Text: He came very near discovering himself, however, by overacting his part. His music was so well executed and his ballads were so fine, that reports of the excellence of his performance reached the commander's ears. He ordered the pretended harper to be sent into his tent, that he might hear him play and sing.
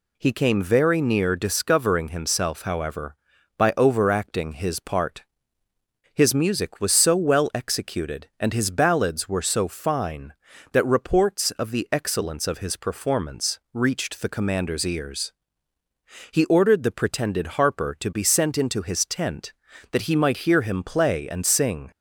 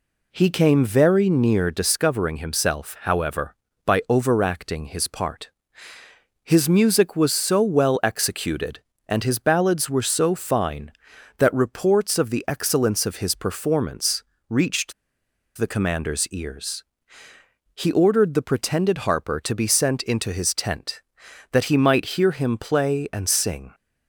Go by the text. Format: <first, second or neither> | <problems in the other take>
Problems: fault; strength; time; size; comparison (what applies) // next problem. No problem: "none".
first | pauses between "performance" and "reached"; slight; at 14.2 s; 0.24 s long // pauses between "reached" and "the"; noticeable; at 14.9 s; 0.63 s long